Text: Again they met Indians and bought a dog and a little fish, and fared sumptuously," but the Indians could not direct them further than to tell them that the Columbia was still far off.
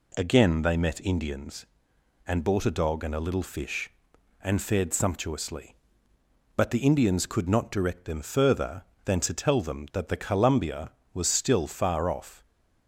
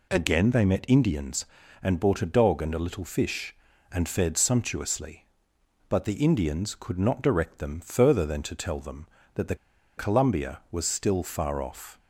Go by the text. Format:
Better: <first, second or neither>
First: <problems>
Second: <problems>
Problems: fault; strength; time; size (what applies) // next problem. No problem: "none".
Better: first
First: none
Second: pauses between "the" and "Columbia"; at 9.5 s; 0.41 s long